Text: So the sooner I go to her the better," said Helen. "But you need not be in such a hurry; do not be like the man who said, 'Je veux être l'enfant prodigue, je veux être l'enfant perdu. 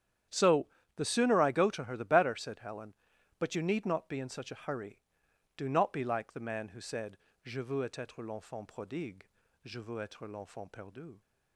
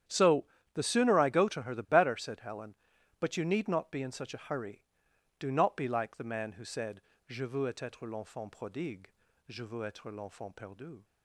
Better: neither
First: starts louder than the rest; strong; until 1.5 s; 10 dB // pauses between "So" and "the"; slight; at 0.6 s; 0.28 s long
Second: starts louder than the rest; strong; until 1.3 s; 10 dB // pauses between "So" and "the"; slight; at 0.4 s; 0.28 s long

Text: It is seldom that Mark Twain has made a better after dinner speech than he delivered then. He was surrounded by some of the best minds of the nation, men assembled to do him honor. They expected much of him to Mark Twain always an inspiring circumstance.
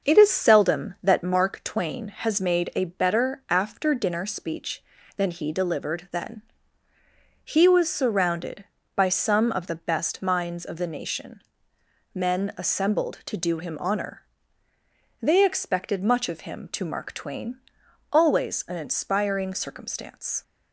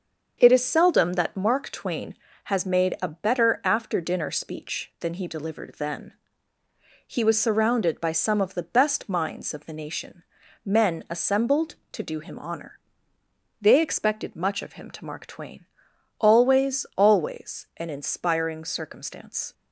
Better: first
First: starts louder than the rest; until 1.1 s; 6.5 dB // pauses between "Twain" and "always"; noticeable; at 17.5 s; 0.54 s long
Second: starts louder than the rest; until 1.3 s; 7 dB // pauses between "Twain" and "always"; noticeable; at 15.6 s; 0.56 s long // says "always" twice; at 16.9 s

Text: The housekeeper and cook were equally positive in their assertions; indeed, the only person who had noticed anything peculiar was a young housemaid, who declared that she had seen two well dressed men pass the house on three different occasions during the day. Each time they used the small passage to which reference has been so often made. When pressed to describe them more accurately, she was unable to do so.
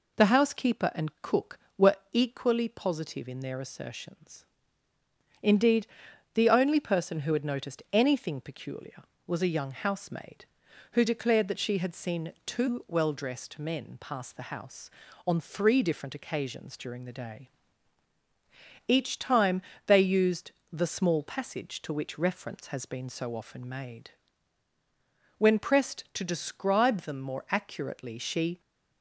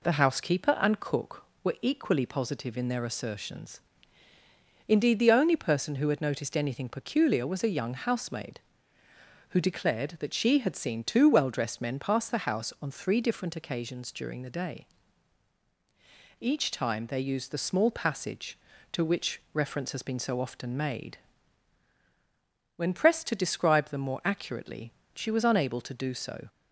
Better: second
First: pauses between "were" and "equally"; slight; at 1.9 s; 0.16 s long // pauses between "time" and "they"; slight; at 19.6 s; 0.24 s long // pauses between "used" and "the"; slight; at 20.5 s; 0.22 s long // stops before "was unable to do so"; at 28.6 s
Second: none

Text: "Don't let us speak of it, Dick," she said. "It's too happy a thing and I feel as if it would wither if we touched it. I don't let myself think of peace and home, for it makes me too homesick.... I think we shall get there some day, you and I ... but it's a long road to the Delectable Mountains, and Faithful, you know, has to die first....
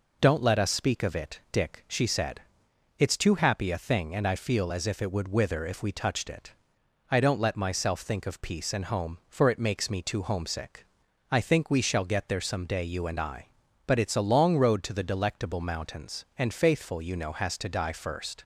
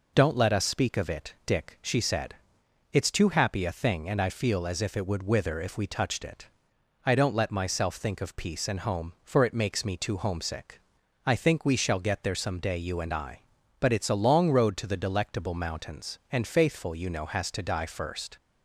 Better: neither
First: none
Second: none

